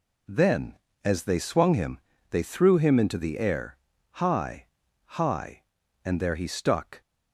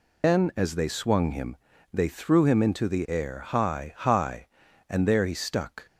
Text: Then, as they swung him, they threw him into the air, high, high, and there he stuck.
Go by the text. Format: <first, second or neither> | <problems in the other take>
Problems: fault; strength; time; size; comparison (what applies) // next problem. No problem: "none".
first | loses the start of "Then"; at 0.2 s; 155 ms